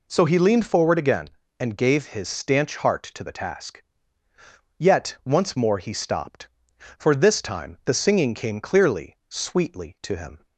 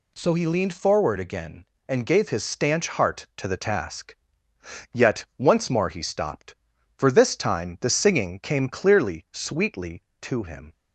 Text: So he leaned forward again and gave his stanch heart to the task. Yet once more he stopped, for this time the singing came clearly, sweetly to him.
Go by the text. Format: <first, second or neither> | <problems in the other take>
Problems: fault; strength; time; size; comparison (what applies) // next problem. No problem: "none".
neither | none